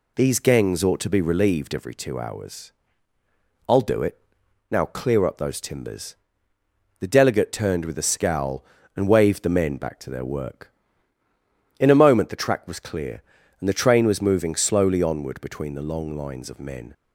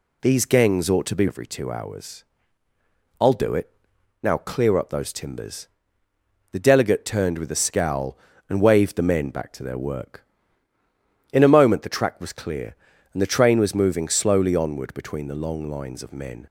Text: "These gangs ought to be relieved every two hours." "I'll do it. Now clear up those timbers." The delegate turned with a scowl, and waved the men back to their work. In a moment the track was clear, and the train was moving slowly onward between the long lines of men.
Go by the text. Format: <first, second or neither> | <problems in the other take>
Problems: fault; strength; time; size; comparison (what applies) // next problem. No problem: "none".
first | skips "relieved"; at 1.2 s